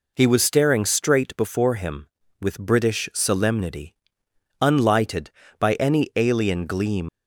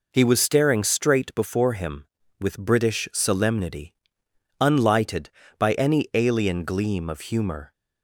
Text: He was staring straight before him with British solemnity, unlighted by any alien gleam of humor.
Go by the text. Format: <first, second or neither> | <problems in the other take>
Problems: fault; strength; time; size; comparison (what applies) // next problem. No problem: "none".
second | stops before "of humor"; at 7.0 s